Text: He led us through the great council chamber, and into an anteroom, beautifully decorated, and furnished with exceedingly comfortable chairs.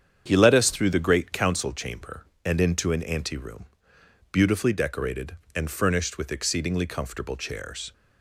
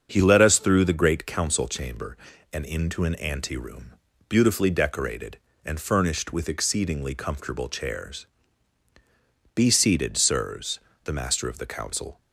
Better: first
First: starts louder than the rest; strong; until 1.2 s; 8 dB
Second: starts louder than the rest; until 1.1 s; 7 dB // goes on to say "Be seated sirs the Master of the Council"; strong; from 9.5 s on; 2.6 s long

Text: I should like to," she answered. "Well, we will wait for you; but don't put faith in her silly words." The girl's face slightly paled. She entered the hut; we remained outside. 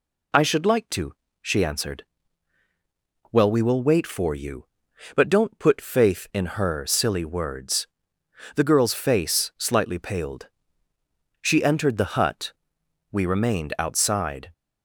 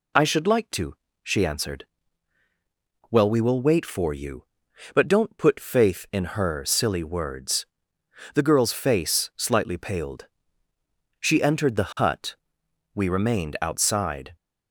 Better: neither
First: none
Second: none

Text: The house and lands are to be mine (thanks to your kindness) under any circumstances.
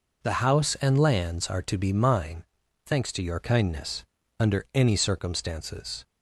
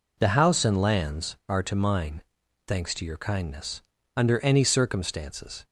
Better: first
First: none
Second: skips "be"; at 1.7 s

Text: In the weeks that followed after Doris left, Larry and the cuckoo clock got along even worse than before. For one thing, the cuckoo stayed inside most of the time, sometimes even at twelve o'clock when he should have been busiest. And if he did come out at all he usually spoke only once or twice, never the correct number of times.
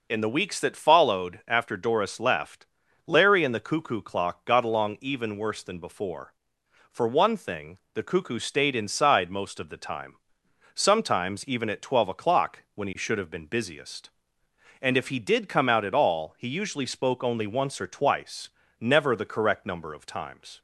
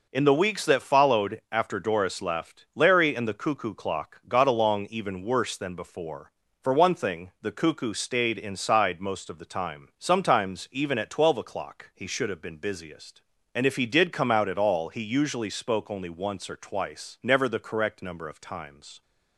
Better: first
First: none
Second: skips "when"; at 11.9 s

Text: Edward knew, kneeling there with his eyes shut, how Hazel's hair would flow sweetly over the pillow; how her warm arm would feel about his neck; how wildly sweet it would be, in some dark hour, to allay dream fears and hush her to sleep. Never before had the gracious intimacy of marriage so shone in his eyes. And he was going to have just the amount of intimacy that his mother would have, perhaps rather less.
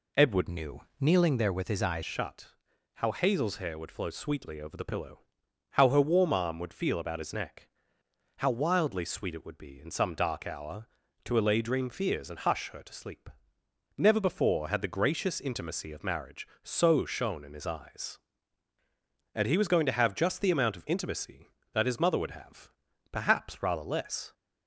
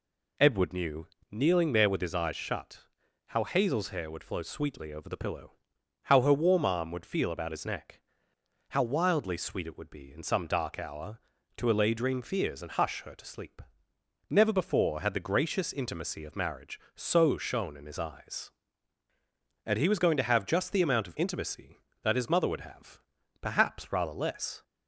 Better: second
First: changes voice from "knew" to "eyes"; from 0.4 to 2.0 s; 1.6 s long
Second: none

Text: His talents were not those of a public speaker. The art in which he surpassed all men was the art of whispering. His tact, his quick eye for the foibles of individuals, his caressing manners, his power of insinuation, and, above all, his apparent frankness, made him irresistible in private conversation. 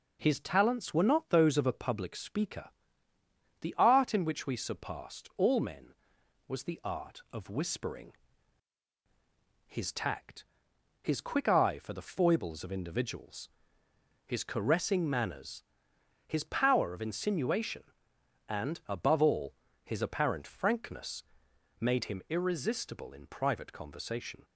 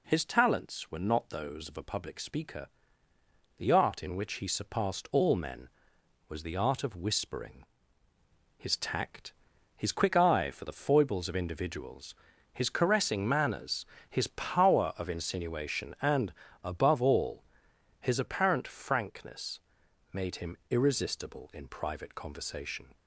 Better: second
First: says "we" for "he"; at 4.4 s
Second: none

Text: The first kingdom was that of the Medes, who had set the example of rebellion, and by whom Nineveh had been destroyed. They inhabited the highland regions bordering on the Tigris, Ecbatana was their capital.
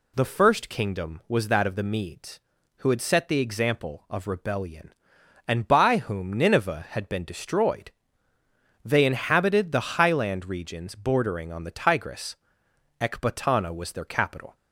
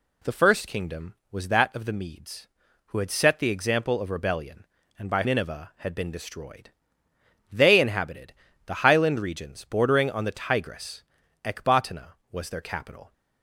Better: first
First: none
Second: skips "whom"; at 5.2 s // pauses between "inhabited" and "the"; slight; at 8.3 s; 0.32 s long

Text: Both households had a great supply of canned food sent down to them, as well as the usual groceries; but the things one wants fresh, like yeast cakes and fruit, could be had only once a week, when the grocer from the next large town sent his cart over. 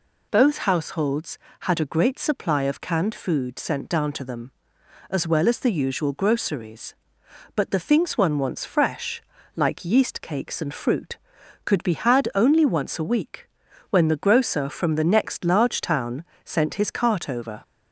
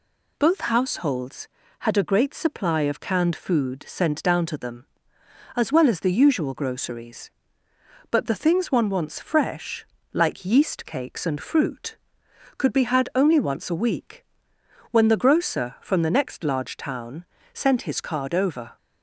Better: first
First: pauses between "town" and "sent"; slight; at 16.2 s; 0.20 s long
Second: pauses between "town" and "sent"; slight; at 17.2 s; 0.26 s long // says "card" for "cart"; at 18.0 s

